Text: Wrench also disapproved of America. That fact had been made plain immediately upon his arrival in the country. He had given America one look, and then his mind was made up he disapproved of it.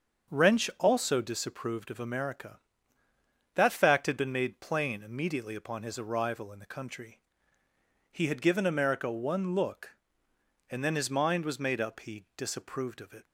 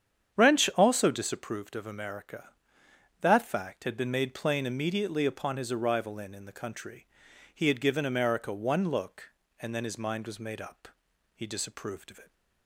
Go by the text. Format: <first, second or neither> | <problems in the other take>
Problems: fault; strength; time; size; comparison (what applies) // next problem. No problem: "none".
first | starts louder than the rest; strong; until 1.4 s; 8.5 dB; also in the first // says "in" twice; at 6.3 s // pauses between "up" and "he"; noticeable; at 10.8 s; 0.46 s long